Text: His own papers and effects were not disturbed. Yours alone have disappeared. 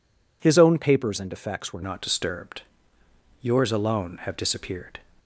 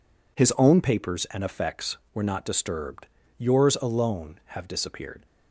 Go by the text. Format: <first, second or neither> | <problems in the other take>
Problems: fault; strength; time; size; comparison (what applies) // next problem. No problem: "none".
second | changes voice at "not"; from 1.8 s on; 3.1 s long